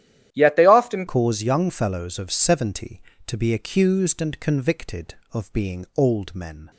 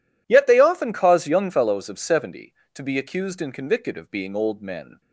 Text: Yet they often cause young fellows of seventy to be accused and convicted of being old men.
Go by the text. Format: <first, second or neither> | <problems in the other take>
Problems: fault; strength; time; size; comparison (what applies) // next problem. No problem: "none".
second | starts louder than the rest; strong; until 1.3 s; 11.5 dB // changes voice at "cause"; from 1.0 s on; 5.7 s long